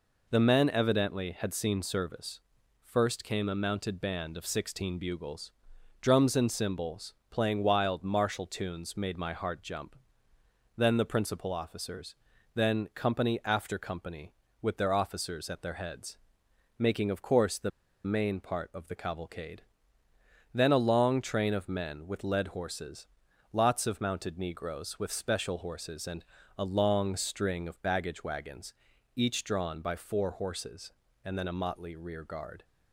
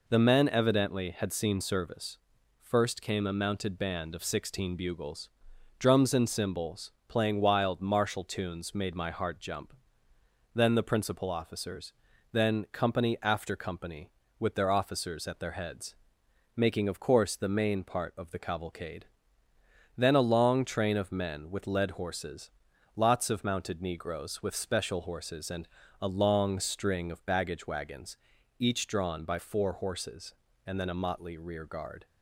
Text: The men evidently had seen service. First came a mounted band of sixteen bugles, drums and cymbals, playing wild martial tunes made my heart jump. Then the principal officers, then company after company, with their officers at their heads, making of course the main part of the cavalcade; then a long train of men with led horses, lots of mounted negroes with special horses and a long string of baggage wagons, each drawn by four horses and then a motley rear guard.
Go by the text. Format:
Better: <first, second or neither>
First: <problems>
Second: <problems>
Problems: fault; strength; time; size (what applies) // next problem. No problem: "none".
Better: second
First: pauses between "the" and "main"; slight; at 17.7 s; 0.35 s long // pauses between "and" and "a"; slight; at 26.2 s; 0.32 s long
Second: pauses between "and" and "a"; slight; at 25.6 s; 0.32 s long